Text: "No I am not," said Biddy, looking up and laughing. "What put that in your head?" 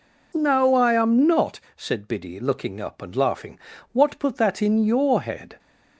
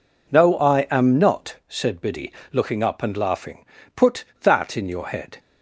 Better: first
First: none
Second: skips "What"; at 3.7 s

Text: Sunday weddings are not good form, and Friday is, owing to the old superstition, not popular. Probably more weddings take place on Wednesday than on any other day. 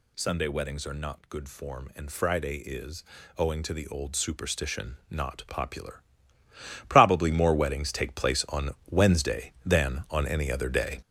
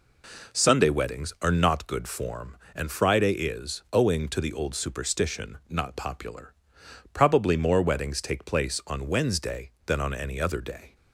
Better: second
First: gets louder; strong; throughout; 8 dB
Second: none

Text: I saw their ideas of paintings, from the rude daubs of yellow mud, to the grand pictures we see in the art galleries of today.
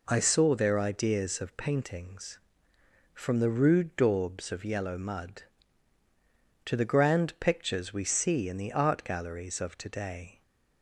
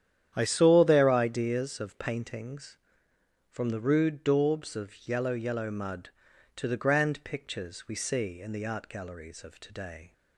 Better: first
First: none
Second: starts louder than the rest; strong; until 1.3 s; 10 dB // says "yellow" twice; at 5.3 s

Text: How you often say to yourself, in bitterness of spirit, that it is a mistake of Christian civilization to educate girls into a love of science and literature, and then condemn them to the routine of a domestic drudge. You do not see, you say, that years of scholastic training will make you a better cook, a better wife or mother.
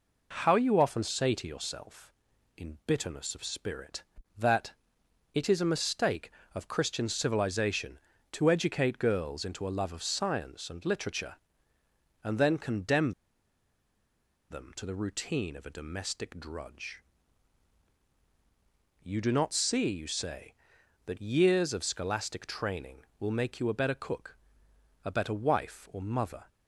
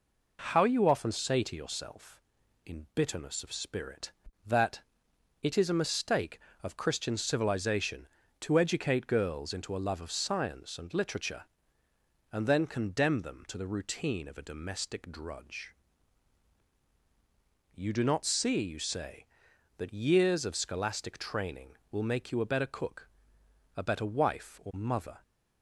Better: second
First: pauses between "that" and "it"; noticeable; at 4.7 s; 0.64 s long // pauses between "condemn" and "them"; strong; at 13.1 s; 1.3 s long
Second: pauses between "that" and "it"; noticeable; at 4.7 s; 0.64 s long

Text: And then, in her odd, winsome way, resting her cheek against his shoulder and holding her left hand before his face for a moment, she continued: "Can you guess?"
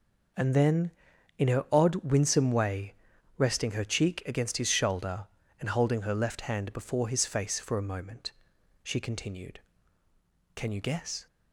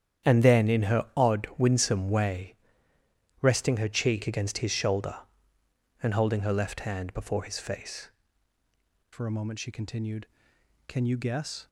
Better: first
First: none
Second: starts louder than the rest; strong; until 1.3 s; 9.5 dB // changes voice at "for"; from 9.1 s on; 2.5 s long

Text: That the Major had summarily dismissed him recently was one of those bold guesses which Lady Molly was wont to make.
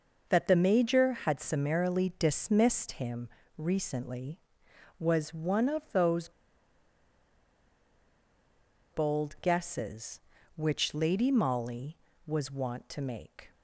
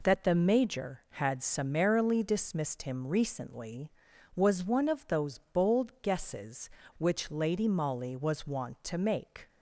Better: second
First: pauses between "him" and "recently"; slight; at 3.2 s; 0.28 s long // pauses between "those" and "bold"; strong; at 6.2 s; 2.6 s long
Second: none

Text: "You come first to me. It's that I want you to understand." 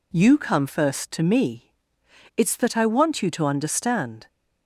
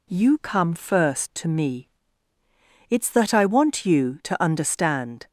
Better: neither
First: none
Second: none

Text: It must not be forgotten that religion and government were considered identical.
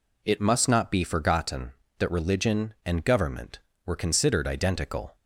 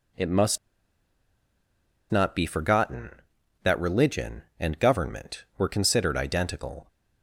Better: first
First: none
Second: pauses between "must" and "not"; strong; at 0.5 s; 1.5 s long

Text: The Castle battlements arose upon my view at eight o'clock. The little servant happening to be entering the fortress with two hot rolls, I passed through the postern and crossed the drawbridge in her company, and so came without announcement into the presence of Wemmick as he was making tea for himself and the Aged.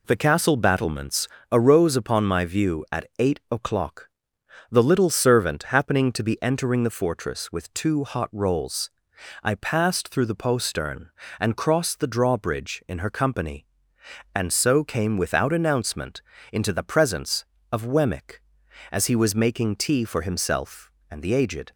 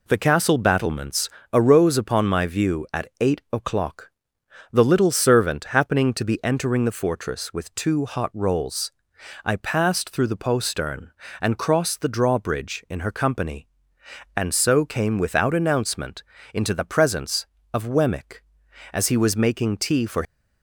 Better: first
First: pauses between "battlements" and "arose"; slight; at 1.2 s; 0.24 s long // pauses between "announcement" and "into"; slight; at 16.2 s; 0.30 s long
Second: pauses between "battlements" and "arose"; slight; at 1.2 s; 0.24 s long // pauses between "announcement" and "into"; slight; at 16.2 s; 0.30 s long // stops before "himself and the Aged"; at 20.2 s

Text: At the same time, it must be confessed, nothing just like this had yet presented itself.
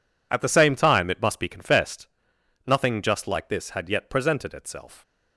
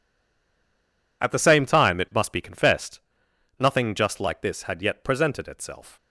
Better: first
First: none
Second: stays silent before the first word; noticeable; until 1.2 s; 1.2 s long

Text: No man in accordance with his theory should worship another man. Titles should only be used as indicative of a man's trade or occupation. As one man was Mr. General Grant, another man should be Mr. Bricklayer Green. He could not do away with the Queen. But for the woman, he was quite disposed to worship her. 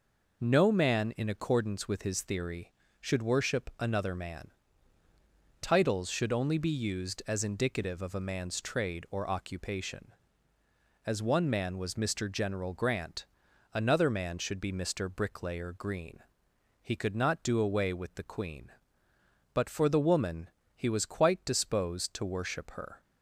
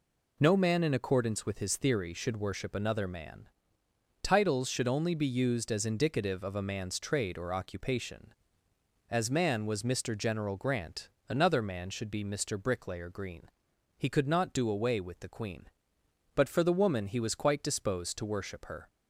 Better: first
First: none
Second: skips "one"; at 9.3 s

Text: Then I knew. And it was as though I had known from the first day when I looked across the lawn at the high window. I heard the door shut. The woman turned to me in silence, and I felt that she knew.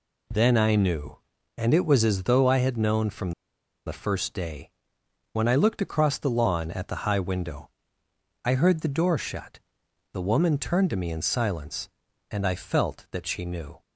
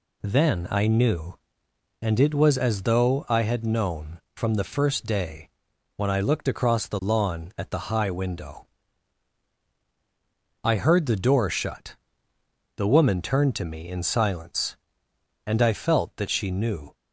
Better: second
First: pauses between "from" and "the"; noticeable; at 3.3 s; 0.55 s long // pauses between "day" and "when"; noticeable; at 4.6 s; 0.64 s long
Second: pauses between "day" and "when"; noticeable; at 5.4 s; 0.46 s long

